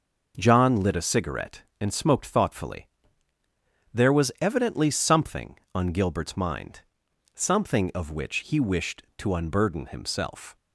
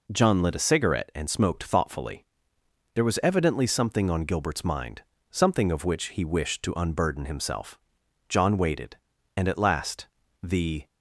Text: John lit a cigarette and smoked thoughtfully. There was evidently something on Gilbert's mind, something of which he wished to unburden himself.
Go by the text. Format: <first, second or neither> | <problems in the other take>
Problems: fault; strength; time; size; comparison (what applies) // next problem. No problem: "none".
first | goes on to say "John waited and at last the"; strong; from 8.2 s on; 2.5 s long